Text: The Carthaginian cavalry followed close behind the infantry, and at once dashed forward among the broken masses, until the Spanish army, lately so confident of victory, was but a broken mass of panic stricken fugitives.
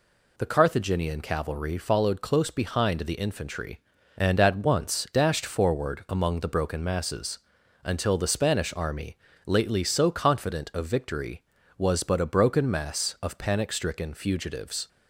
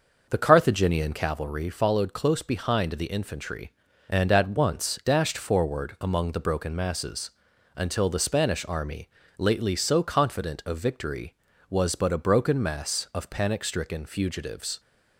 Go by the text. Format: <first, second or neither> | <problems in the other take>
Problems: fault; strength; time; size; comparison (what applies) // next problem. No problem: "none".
first | starts louder than the rest; noticeable; until 1.4 s; 6 dB